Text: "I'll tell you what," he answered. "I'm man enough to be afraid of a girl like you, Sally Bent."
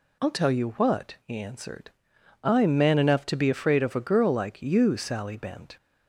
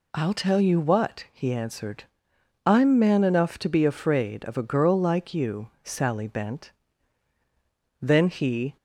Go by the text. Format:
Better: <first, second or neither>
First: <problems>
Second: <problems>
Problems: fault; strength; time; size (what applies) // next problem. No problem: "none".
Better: first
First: none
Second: goes on to say "Then he"; noticeable; from 8.0 s on; 0.74 s long